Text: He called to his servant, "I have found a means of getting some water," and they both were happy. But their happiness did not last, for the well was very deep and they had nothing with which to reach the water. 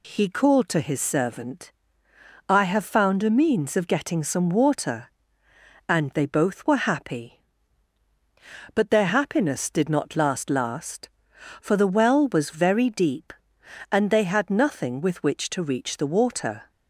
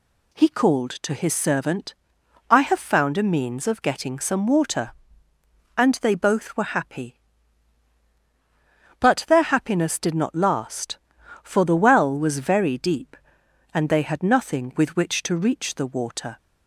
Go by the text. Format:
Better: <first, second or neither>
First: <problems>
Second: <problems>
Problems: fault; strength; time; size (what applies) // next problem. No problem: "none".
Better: second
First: says "last" twice; at 10.4 s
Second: none